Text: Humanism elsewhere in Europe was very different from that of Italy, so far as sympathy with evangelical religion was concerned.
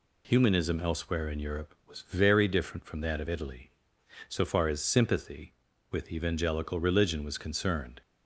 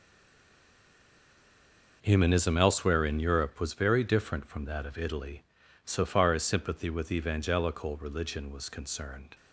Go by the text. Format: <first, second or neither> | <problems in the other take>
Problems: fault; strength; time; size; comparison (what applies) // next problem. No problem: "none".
first | stays silent before the first word; noticeable; until 2.0 s; 2.0 s long